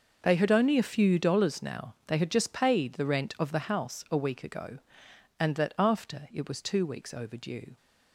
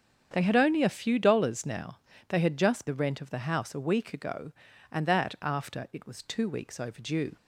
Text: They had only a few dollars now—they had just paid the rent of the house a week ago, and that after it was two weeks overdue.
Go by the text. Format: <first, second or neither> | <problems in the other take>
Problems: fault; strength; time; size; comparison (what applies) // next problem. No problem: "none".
first | starts louder than the rest; strong; until 1.3 s; 7.5 dB // skips "paid"; at 2.8 s